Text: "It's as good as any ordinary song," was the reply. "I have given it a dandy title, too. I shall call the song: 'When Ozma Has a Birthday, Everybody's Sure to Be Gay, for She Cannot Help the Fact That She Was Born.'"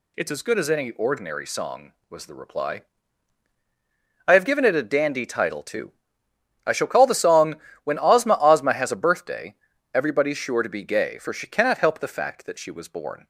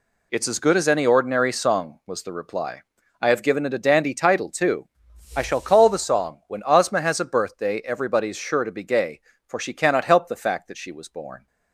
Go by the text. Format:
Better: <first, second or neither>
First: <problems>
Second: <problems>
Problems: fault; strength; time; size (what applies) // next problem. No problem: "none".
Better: second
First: says "Ozma" twice; at 8.3 s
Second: none